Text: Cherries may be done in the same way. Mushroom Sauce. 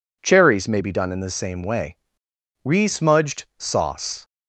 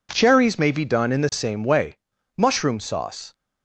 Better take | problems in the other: second | says "Resmudged" for "Mushroom"; at 2.6 s

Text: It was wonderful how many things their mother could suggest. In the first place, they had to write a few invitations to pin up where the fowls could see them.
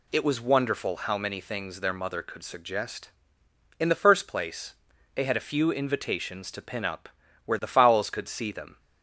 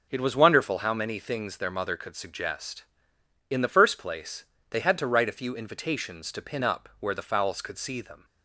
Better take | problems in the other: second | skips "to write"; at 5.3 s // pauses between "up" and "where"; slight; at 7.0 s; 0.36 s long

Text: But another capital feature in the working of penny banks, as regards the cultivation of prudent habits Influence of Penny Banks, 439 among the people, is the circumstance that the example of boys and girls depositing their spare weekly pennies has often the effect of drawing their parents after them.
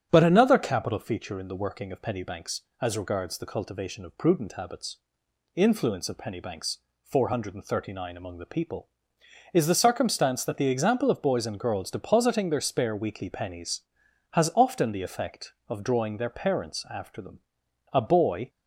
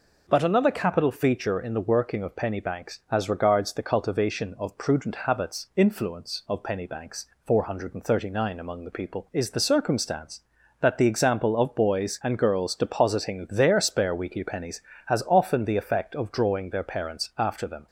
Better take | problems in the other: second | starts louder than the rest; strong; until 1.1 s; 8 dB // pauses between "habits" and "Influence"; noticeable; at 4.9 s; 0.58 s long // goes on to say "A boy"; from 17.9 s on; 0.56 s long

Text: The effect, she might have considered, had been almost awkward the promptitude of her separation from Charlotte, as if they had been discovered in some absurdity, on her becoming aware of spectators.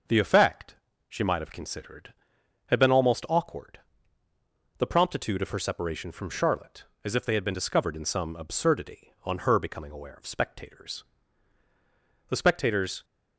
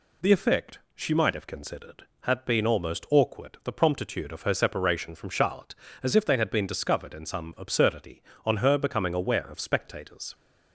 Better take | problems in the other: second | starts louder than the rest; until 1.4 s; 6 dB // pauses between "awkward" and "the"; at 3.7 s; 1.0 s long // goes on to say "The spectators"; noticeable; from 12.2 s on; 0.74 s long

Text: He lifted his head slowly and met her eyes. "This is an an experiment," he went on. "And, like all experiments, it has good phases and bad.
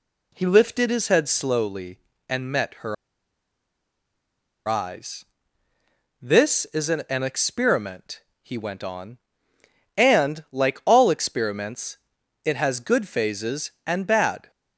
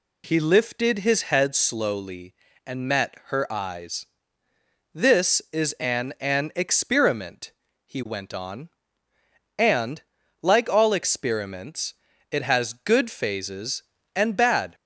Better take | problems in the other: second | pauses between "her" and "eyes"; strong; at 2.9 s; 1.7 s long

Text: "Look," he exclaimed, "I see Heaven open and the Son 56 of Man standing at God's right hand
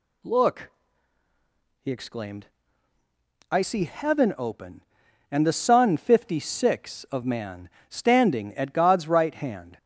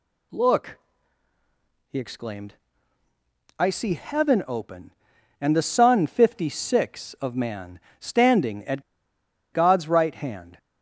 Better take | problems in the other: first | pauses between "Man" and "standing"; slight; at 7.7 s; 0.22 s long; slight in the first // pauses between "at" and "God's"; noticeable; at 8.8 s; 0.71 s long

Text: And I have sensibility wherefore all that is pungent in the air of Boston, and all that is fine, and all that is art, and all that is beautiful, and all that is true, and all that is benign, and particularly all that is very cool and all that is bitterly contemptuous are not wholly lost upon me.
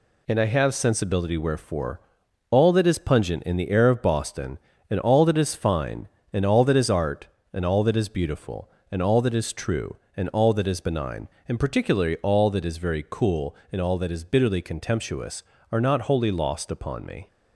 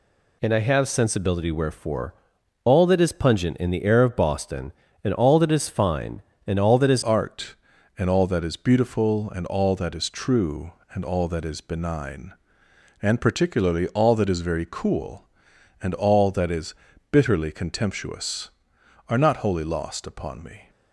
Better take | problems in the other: first | pauses between "wherefore" and "all"; noticeable; at 2.1 s; 0.50 s long; noticeable in the first // changes voice at "art"; from 7.0 s on; 13.6 s long // pauses between "is" and "bitterly"; slight; at 16.7 s; 0.36 s long

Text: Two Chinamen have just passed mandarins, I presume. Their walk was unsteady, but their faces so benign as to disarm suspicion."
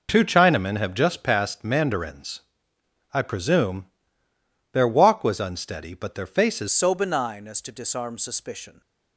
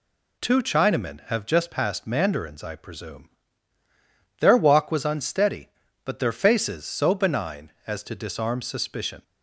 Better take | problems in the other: second | changes voice at "so"; from 6.7 s on; 2.1 s long

